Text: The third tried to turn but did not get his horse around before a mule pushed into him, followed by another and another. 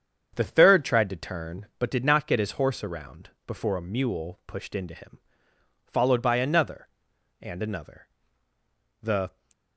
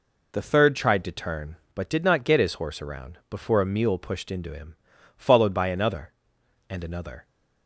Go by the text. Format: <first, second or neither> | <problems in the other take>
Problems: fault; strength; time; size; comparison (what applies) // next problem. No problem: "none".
second | starts louder than the rest; strong; until 1.3 s; 7.5 dB // pauses between "around" and "before"; slight; at 3.3 s; 0.16 s long // goes on to say "The"; slight; from 9.0 s on; 0.32 s long